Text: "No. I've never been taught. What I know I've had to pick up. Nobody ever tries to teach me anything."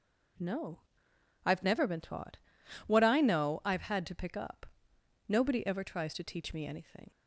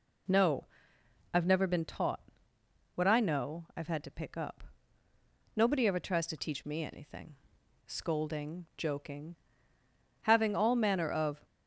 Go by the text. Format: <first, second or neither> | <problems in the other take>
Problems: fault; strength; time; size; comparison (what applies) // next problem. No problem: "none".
first | goes on to say "Scolding joking having all manner of"; strong; from 7.8 s on; 3.6 s long